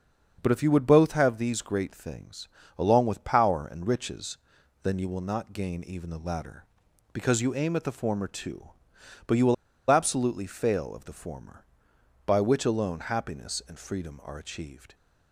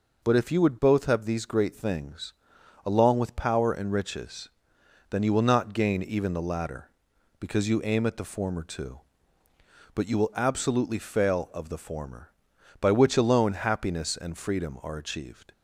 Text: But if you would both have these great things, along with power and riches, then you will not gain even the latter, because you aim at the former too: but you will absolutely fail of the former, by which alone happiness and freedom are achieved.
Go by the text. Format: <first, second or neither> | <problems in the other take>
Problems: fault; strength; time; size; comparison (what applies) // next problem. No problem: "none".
second | starts louder than the rest; strong; until 1.4 s; 7.5 dB // pauses between "will" and "absolutely"; slight; at 9.5 s; 0.35 s long